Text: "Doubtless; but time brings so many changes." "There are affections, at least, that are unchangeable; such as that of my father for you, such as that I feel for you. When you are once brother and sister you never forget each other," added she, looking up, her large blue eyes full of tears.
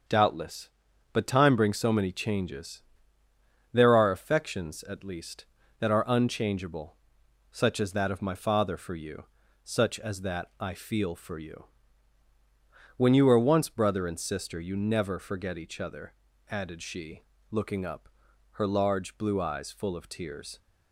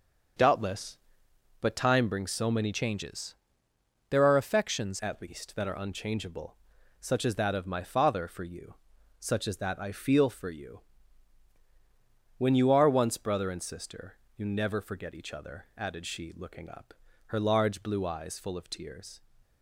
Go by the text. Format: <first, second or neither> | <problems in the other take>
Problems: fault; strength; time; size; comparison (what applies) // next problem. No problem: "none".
first | starts louder than the rest; until 2.0 s; 7 dB; also in the first // changes voice from "changes" to "affections"; from 2.7 to 4.9 s; 2.2 s long // pauses between "sister" and "you"; slight; at 14.1 s; 0.18 s long